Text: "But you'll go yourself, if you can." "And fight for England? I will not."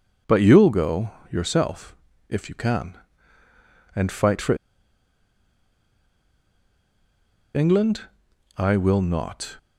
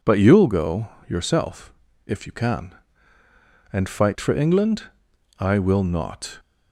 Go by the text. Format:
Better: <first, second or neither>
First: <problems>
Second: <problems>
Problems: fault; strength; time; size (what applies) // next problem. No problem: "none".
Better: second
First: pauses between "go" and "yourself"; slight; at 1.1 s; 0.22 s long // pauses between "for" and "England"; strong; at 4.5 s; 3.0 s long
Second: pauses between "go" and "yourself"; slight; at 0.8 s; 0.22 s long